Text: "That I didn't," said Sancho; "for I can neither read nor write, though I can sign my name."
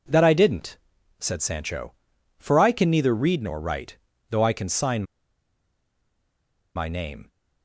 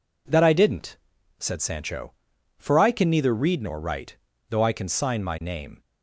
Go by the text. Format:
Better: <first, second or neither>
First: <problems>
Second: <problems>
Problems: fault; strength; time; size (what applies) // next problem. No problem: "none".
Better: second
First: pauses between "sign" and "my"; strong; at 5.0 s; 1.7 s long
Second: none